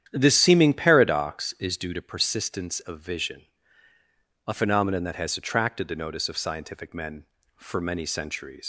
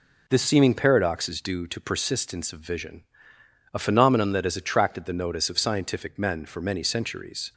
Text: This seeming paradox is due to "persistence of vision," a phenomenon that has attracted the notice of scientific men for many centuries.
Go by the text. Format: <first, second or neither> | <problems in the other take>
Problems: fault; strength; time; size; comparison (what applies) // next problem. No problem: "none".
second | starts louder than the rest; strong; until 1.1 s; 9.5 dB // leaves "centuries" unfinished; at 8.6 s; 90 ms